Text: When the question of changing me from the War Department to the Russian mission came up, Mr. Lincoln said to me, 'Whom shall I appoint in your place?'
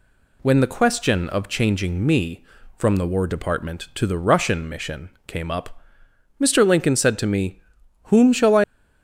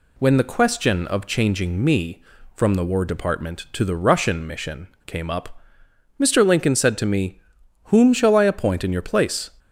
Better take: second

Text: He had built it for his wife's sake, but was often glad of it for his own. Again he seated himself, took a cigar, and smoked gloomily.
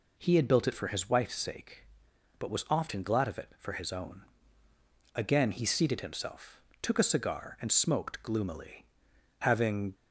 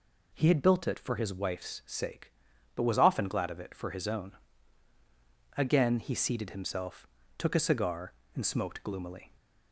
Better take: second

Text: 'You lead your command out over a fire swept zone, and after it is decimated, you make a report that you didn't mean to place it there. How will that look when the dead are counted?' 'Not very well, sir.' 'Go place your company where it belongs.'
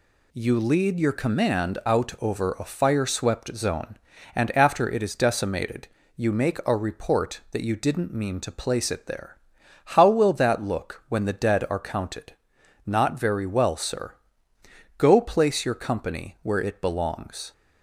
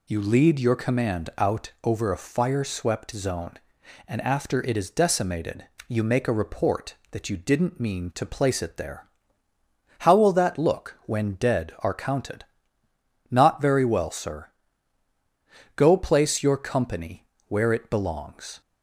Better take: first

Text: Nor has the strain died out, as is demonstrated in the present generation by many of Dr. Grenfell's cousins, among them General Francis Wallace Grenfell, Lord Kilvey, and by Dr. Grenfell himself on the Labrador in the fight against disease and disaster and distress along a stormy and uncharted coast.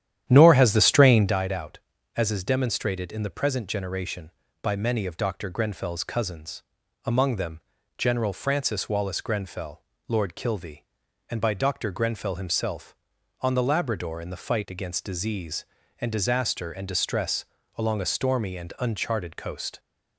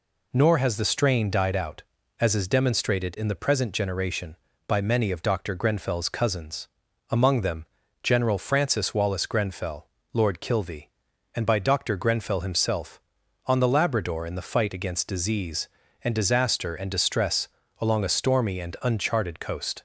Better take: second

